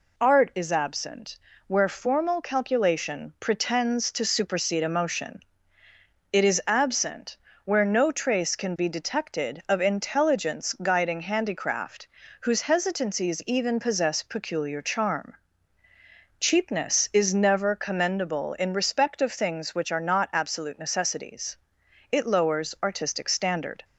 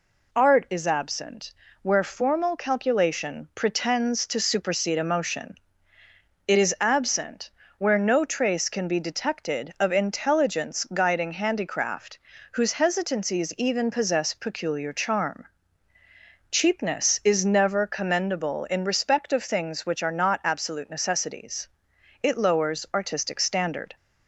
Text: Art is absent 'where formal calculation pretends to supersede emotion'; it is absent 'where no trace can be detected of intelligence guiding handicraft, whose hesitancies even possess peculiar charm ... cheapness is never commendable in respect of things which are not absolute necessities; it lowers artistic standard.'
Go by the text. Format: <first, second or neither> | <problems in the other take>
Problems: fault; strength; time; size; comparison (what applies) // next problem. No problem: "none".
neither | pauses between "absent" and "where"; slight; the same in both // pauses between "absent" and "where"; slight; the same in both